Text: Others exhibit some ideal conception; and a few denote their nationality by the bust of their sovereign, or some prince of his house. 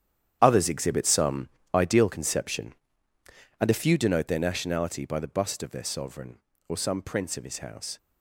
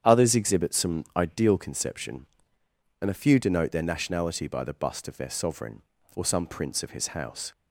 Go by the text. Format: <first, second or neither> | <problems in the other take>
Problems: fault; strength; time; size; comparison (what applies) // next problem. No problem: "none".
second | gets quieter; strong; throughout; 11.5 dB // starts louder than the rest; strong; until 1.4 s; 9.5 dB; strong in the second // pauses between "some" and "ideal"; slight; at 1.4 s; 0.24 s long